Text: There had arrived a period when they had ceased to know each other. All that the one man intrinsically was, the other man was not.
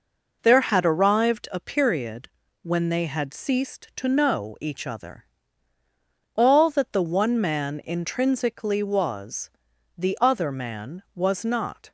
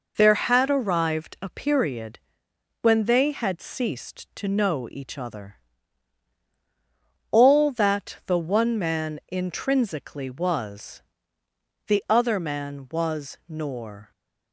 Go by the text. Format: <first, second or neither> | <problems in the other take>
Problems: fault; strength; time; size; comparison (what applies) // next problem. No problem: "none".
first | pauses between "period" and "when"; noticeable; at 2.1 s; 0.62 s long; slight in the first // says "nor" for "not"; at 13.4 s